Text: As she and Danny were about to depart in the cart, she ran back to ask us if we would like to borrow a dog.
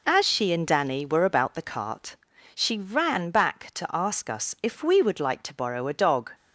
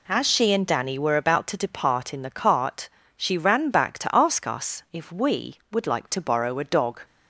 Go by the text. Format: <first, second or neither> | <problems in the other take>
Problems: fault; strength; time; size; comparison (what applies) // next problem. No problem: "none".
second | skips "to depart in"; at 1.5 s